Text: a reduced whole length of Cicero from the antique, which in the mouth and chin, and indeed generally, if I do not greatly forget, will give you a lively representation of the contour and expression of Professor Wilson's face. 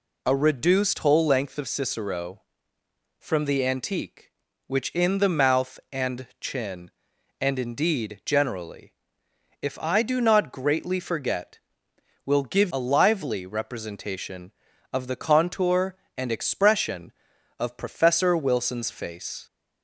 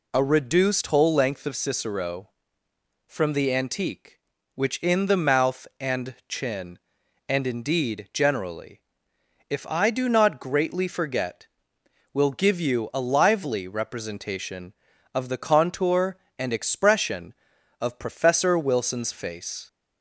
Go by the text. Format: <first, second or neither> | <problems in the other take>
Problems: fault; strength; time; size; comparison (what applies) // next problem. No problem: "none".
second | skips "you"; at 12.7 s